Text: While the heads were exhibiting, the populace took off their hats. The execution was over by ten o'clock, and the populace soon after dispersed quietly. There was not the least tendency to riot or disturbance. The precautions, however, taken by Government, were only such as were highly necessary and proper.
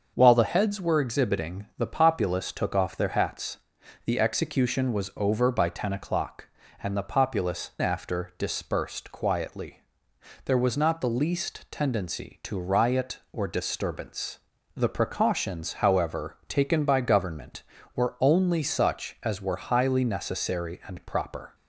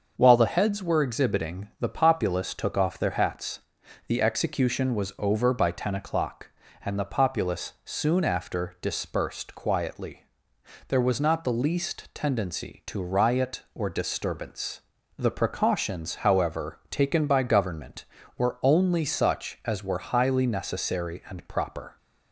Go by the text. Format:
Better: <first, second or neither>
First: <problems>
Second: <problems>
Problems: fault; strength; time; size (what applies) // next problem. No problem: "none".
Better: second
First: starts louder than the rest; until 1.1 s; 6.5 dB // skips "soon"; at 7.7 s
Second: starts louder than the rest; until 1.1 s; 6.5 dB